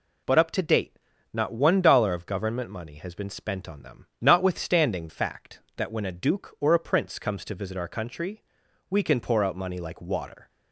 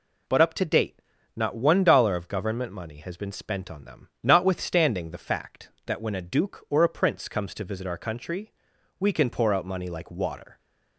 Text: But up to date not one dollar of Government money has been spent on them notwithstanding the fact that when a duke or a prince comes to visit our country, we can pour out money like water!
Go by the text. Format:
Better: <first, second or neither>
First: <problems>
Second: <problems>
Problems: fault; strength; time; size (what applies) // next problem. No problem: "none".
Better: second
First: pauses between "date" and "not"; at 0.9 s; 0.38 s long // pauses between "them" and "notwithstanding"; slight; at 4.0 s; 0.16 s long // skips "the"; at 5.0 s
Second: pauses between "date" and "not"; at 1.0 s; 0.38 s long // pauses between "them" and "notwithstanding"; slight; at 4.0 s; 0.16 s long